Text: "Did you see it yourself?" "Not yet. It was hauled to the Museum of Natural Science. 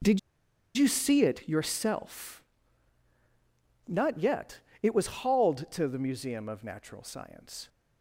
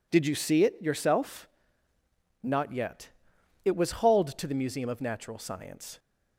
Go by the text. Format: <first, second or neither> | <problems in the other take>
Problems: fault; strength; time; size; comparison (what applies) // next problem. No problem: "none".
second | starts louder than the rest; strong; until 1.6 s; 8 dB // pauses between "Did" and "you"; noticeable; at 0.1 s; 0.56 s long // pauses between "was" and "hauled"; slight; at 5.0 s; 0.16 s long